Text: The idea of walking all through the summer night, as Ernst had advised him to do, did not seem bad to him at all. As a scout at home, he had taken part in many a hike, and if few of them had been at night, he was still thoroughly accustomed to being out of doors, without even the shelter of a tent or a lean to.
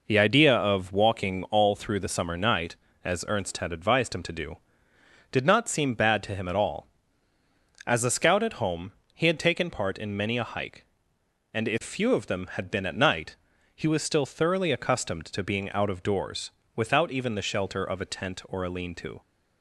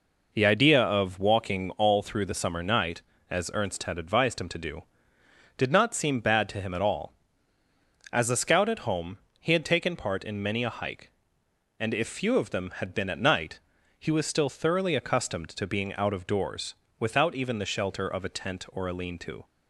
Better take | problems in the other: neither | none

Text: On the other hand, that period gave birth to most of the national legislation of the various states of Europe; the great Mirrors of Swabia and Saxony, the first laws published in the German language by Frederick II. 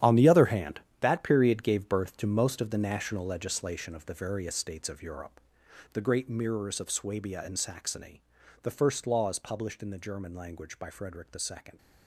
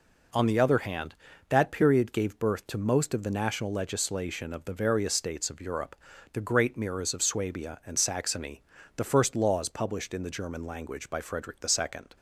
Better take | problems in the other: second | gets quieter; strong; throughout; 13 dB

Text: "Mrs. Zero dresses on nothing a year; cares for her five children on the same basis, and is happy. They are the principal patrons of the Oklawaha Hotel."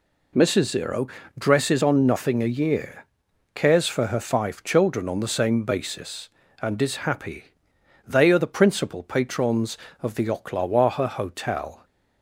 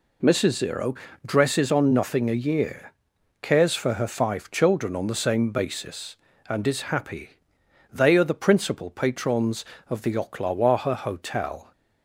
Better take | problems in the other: neither | pauses between "Zero" and "dresses"; slight; the same in both

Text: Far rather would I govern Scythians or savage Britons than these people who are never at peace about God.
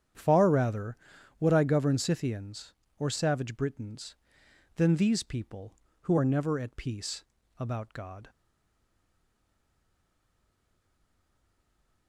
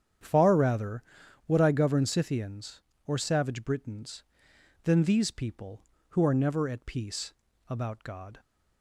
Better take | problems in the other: second | starts louder than the rest; strong; until 1.5 s; 9 dB; strong in the second // pauses between "peace" and "about"; slight; at 7.2 s; 0.35 s long; slight in the second // stays silent after the last word; strong; from 8.2 s on; 3.8 s long

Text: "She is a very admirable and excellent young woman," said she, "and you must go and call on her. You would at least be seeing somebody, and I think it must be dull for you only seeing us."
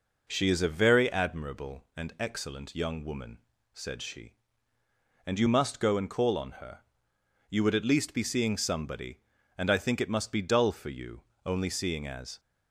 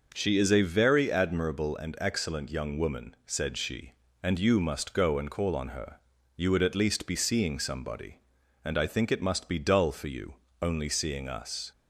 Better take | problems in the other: second | pauses between "you" and "only"; slight; at 11.2 s; 0.24 s long; slight in the second // says "as" for "us"; at 12.0 s

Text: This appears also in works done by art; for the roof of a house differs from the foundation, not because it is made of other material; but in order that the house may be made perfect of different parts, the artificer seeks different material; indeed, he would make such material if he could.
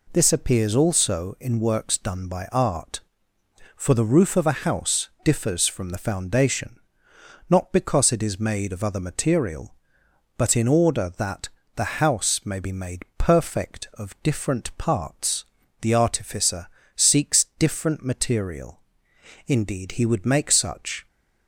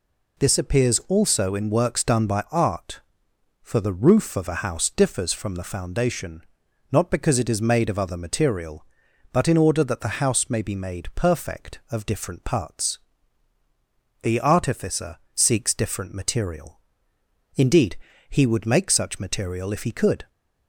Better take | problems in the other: second | pauses between "that" and "the"; slight; at 11.4 s; 0.26 s long // pauses between "artificer" and "seeks"; slight; at 16.6 s; 0.28 s long; slight in the second // stops before "material if he could"; at 21.0 s

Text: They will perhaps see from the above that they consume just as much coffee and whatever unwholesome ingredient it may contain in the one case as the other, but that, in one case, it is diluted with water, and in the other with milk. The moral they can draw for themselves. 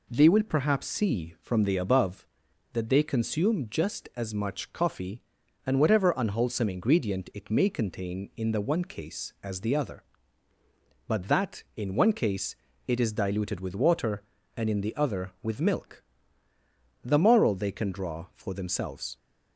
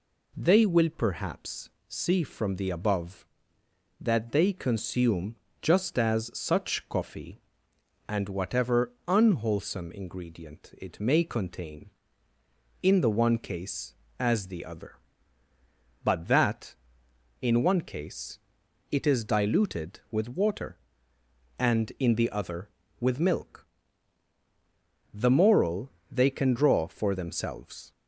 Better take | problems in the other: first | pauses between "perhaps" and "see"; slight; at 1.6 s; 0.18 s long // pauses between "consume" and "just"; slight; at 5.3 s; 0.26 s long // says "such" for "much"; at 6.3 s // pauses between "moral" and "they"; slight; at 25.9 s; 0.18 s long

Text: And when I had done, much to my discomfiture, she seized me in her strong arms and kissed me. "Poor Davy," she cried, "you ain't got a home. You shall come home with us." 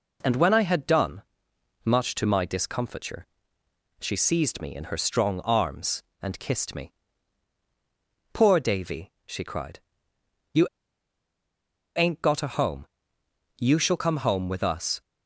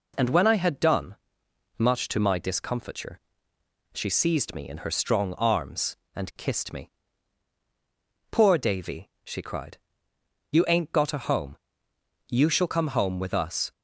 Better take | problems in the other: second | pauses between "you" and "ain't"; strong; at 10.6 s; 1.2 s long

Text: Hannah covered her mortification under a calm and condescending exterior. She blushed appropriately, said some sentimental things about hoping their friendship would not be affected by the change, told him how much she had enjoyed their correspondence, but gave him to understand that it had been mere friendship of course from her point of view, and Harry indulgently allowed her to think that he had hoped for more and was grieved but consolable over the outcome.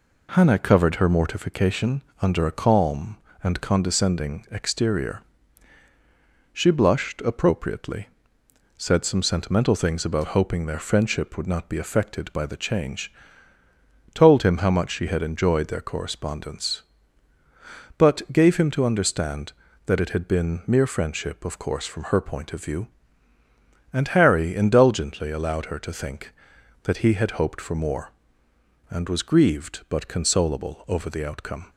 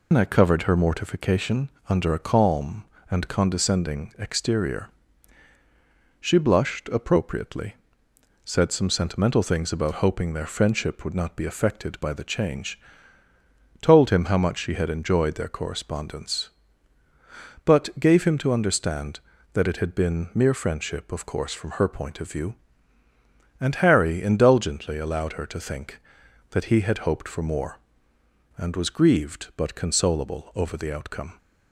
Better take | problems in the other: first | loses the start of "Hannah"; at 0.1 s; 150 ms // pauses between "mortification" and "under"; slight; at 1.7 s; 0.18 s long; slight in the first

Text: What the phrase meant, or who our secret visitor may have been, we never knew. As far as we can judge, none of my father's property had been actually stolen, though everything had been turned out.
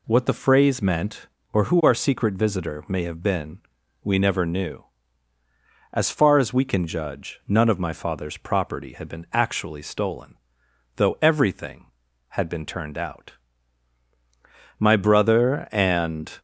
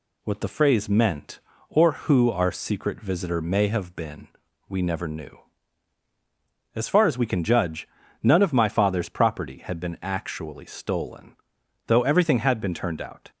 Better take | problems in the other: second | goes on to say "My brother and"; from 14.7 s on; 1.5 s long

